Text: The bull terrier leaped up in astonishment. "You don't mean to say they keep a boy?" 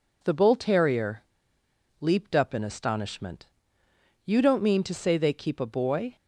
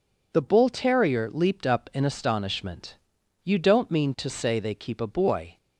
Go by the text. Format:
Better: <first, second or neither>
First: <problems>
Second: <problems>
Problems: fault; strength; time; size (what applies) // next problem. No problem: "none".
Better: second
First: pauses between "terrier" and "leaped"; noticeable; at 1.2 s; 0.76 s long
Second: none